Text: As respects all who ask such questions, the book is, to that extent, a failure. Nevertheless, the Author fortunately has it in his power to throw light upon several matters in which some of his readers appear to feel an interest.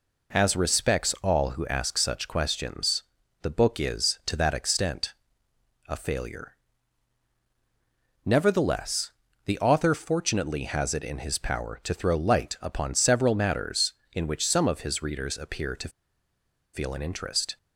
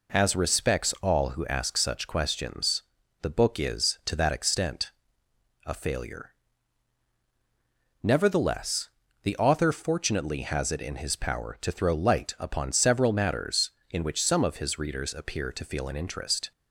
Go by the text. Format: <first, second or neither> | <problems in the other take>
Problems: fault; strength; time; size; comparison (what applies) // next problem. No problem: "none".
second | pauses between "to" and "feel"; noticeable; at 15.8 s; 0.84 s long